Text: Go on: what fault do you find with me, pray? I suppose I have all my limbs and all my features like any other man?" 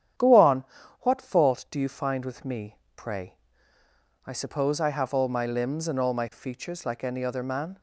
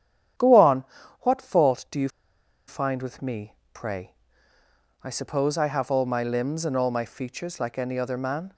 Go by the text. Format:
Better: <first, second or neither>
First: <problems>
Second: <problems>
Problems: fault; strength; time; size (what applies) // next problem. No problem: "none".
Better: first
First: starts louder than the rest; strong; until 1.5 s; 9.5 dB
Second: starts louder than the rest; strong; until 1.7 s; 9.5 dB // pauses between "you" and "find"; noticeable; at 2.0 s; 0.58 s long